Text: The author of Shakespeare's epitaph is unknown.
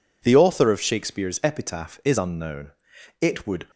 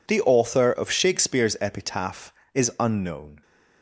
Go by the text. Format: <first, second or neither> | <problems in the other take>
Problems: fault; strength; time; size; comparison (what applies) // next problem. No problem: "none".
second | goes on to say "It would"; slight; from 3.2 s on; 0.48 s long